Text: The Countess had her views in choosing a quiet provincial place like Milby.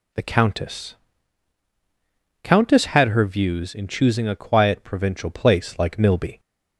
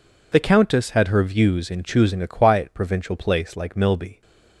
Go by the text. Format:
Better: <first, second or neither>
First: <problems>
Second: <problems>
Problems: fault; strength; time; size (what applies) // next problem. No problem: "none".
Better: second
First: says "Countess" twice; at 2.4 s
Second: none